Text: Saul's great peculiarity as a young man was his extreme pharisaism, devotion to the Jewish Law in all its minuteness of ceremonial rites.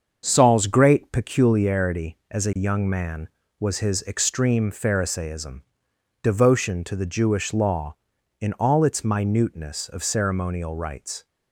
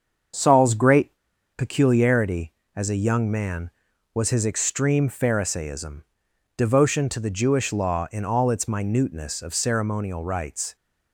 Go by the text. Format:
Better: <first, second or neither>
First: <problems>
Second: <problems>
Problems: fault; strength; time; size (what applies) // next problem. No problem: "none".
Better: first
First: starts louder than the rest; until 1.2 s; 6.5 dB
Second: starts louder than the rest; until 1.8 s; 7 dB // pauses between "great" and "peculiarity"; at 1.1 s; 0.44 s long